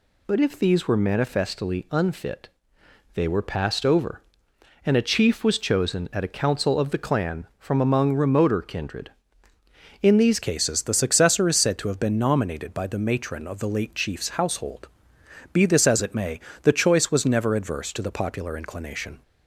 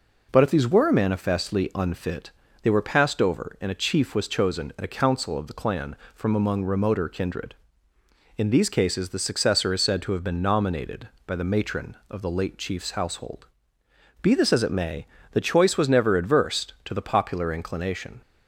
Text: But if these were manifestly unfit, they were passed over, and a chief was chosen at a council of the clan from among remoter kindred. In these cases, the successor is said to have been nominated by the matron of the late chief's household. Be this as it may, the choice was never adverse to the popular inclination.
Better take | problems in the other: second | changes voice at "cases"; from 10.4 s on; 8.8 s long

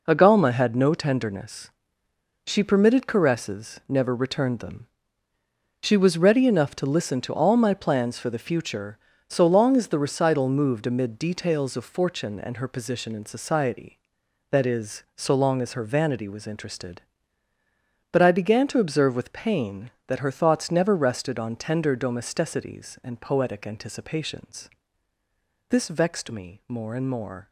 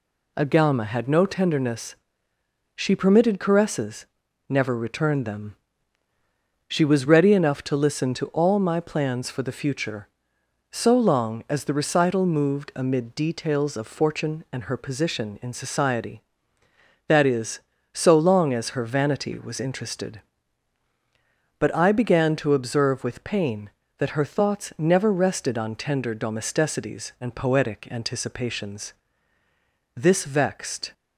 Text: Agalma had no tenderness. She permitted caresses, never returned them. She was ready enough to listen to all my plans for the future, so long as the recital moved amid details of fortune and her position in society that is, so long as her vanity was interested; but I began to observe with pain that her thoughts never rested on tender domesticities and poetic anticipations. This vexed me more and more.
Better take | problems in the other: first | stops before "me more and more"; at 30.9 s

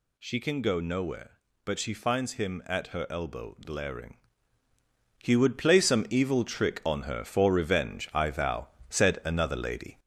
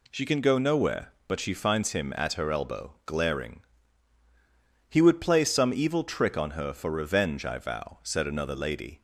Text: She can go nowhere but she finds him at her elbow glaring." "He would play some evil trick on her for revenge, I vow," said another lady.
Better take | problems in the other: second | gets louder; slight; throughout; 3 dB

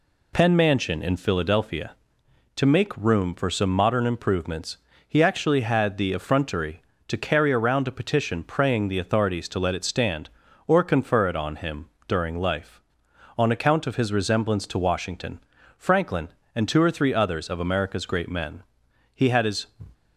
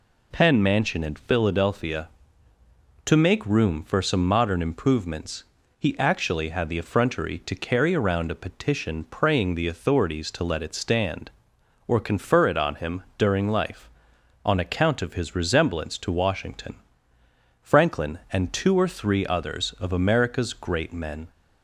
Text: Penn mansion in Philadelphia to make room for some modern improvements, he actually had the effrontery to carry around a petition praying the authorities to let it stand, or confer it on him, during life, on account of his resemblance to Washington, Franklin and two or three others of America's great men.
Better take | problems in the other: second | goes on to say "He had his"; from 19.1 s on; 0.50 s long

